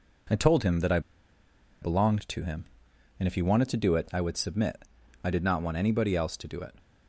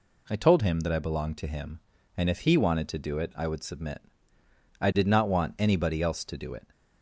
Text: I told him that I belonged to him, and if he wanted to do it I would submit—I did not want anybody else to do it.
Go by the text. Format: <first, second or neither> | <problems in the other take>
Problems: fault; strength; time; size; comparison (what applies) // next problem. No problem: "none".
second | pauses between "I" and "belonged"; noticeable; at 0.9 s; 0.81 s long